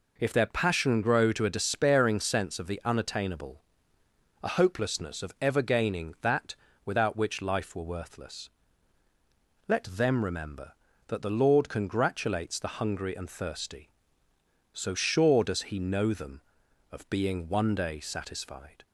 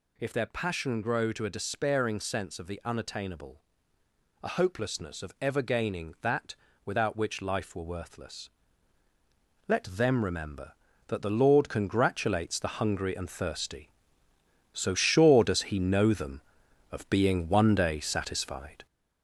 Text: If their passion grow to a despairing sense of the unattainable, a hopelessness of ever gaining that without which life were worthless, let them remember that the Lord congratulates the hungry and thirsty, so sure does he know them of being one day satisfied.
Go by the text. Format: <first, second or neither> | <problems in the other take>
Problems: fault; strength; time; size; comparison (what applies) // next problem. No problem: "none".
first | gets louder; noticeable; throughout; 4.5 dB // pauses between "that" and "without"; slight; at 6.5 s; 0.30 s long; slight in the first